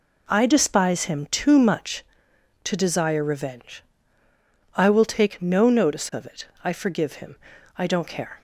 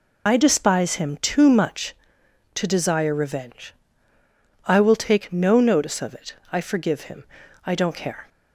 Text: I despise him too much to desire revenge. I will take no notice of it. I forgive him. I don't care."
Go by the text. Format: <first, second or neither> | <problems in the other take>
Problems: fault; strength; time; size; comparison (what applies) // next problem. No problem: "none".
first | loses the start of "I"; at 0.2 s; 65 ms